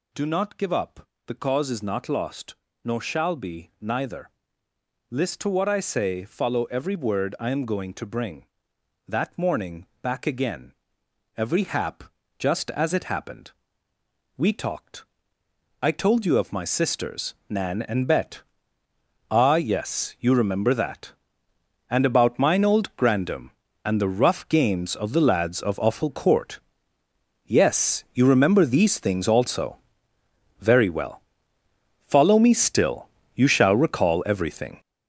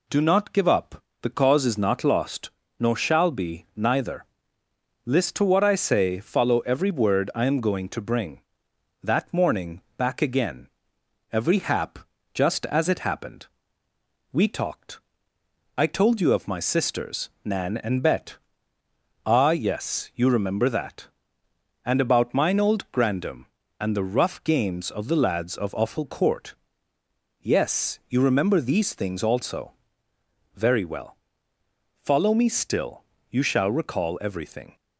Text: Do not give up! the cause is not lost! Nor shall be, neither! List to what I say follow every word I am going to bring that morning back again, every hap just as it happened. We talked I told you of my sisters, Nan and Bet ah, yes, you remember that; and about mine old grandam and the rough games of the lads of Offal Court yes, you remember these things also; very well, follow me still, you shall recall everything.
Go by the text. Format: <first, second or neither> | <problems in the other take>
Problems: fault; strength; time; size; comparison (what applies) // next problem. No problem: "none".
second | gets louder; strong; throughout; 9 dB // pauses between "morning" and "back"; slight; at 9.8 s; 0.16 s long; slight in the second // pauses between "hap" and "just"; slight; at 12.0 s; 0.34 s long; slight in the second // pauses between "talked" and "I"; noticeable; at 15.0 s; 0.78 s long; noticeable in the second // pauses between "Bet" and "ah"; noticeable; at 18.4 s; 0.88 s long; noticeable in the second // pauses between "Court" and "yes"; noticeable; at 26.5 s; 0.86 s long; noticeable in the second